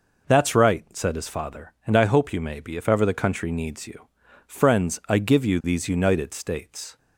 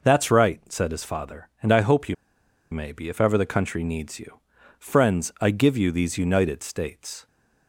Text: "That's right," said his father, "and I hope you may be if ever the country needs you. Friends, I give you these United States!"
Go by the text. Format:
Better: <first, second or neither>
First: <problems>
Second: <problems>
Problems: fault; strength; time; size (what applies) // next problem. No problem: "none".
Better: first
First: none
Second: pauses between "you" and "may"; noticeable; at 2.1 s; 0.56 s long